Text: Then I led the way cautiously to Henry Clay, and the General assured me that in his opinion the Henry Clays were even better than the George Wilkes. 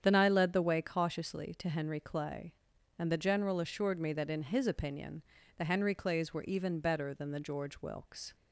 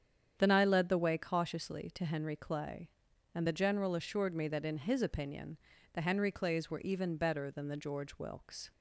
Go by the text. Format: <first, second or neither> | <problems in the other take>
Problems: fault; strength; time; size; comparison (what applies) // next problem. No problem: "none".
neither | starts louder than the rest; strong; the same in both // pauses between "opinion" and "the"; slight; the same in both